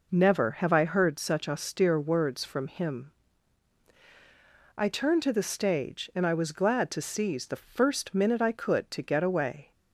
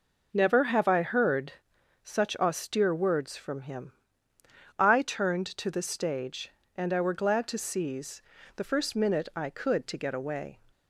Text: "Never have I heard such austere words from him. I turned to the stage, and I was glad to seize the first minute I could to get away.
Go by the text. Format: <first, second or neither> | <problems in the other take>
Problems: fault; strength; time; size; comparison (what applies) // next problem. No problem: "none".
first | pauses between "heard" and "such"; noticeable; at 1.5 s; 0.54 s long // says "were" for "was"; at 7.0 s // pauses between "seize" and "the"; slight; at 8.2 s; 0.36 s long